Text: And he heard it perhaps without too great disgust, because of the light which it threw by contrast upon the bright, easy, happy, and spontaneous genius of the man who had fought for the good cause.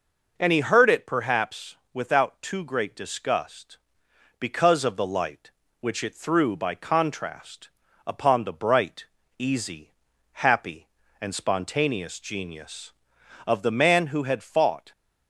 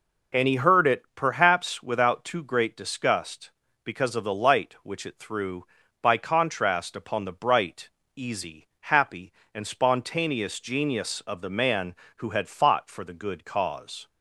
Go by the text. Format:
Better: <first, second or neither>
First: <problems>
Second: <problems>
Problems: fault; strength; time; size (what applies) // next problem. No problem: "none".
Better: second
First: pauses between "perhaps" and "without"; slight; at 1.7 s; 0.18 s long // pauses between "contrast" and "upon"; slight; at 7.6 s; 0.36 s long // stops before "for the good cause"; at 14.9 s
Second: none